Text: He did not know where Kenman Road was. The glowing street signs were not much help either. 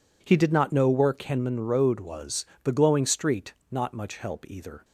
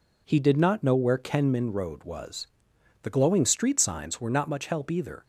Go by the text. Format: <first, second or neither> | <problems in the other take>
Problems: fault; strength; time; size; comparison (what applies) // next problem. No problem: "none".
second | skips "signs were"; at 3.6 s